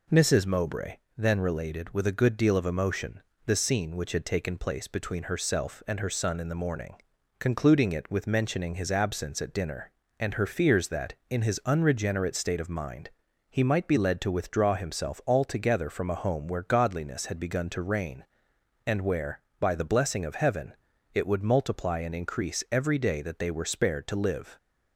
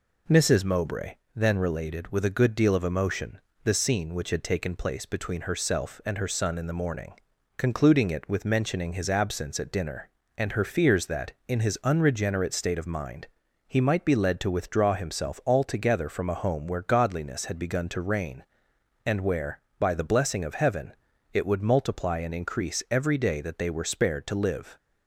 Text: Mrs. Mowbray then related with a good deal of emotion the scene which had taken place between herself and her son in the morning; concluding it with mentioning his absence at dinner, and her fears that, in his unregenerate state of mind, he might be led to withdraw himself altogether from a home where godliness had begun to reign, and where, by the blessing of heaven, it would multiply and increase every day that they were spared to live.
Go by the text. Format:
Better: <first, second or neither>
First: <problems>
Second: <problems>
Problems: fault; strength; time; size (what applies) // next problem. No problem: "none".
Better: neither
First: pauses between "Mowbray" and "then"; slight; at 0.9 s; 0.22 s long // pauses between "emotion" and "the"; slight; at 3.2 s; 0.24 s long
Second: pauses between "Mowbray" and "then"; slight; at 1.1 s; 0.22 s long // pauses between "emotion" and "the"; slight; at 3.3 s; 0.24 s long